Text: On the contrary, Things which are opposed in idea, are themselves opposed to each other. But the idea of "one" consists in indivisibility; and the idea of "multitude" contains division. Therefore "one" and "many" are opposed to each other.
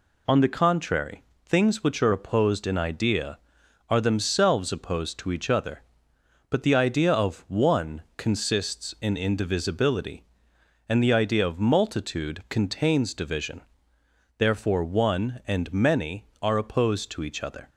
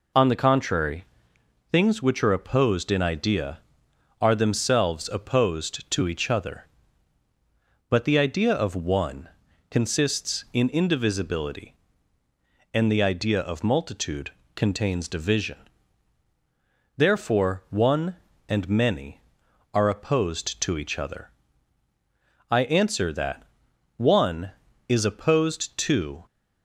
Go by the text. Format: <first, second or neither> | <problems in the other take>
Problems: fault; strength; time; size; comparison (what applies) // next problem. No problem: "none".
first | pauses between "one" and "consists"; at 9.3 s; 0.40 s long; slight in the first // pauses between "multitude" and "contains"; slight; at 14.3 s; 0.22 s long // goes on to say "I answer that One is opposed to"; strong; from 22.5 s on; 3.7 s long